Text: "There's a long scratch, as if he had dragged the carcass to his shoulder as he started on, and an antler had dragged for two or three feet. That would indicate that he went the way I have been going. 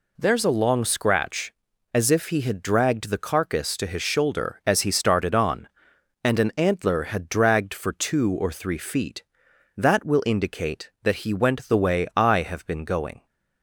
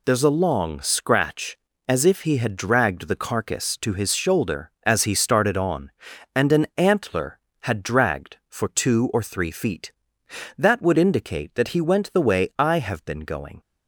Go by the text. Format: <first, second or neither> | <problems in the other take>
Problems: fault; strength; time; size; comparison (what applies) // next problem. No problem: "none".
second | says "will" for "would"; at 10.0 s